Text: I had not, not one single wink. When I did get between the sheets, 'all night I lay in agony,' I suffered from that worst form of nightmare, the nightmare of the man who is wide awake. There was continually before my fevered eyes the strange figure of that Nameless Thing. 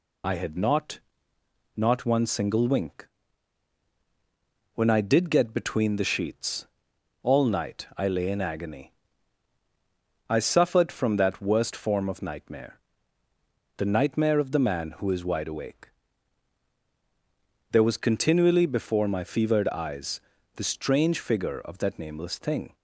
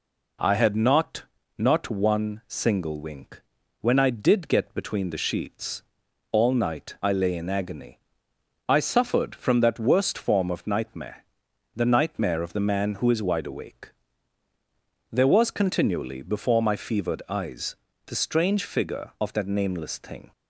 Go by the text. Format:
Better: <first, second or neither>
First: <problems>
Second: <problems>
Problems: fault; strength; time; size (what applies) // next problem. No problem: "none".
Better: second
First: loses the start of "I"; at 0.2 s; 40 ms // pauses between "eyes" and "the"; at 20.1 s; 0.38 s long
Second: pauses between "eyes" and "the"; slight; at 17.7 s; 0.30 s long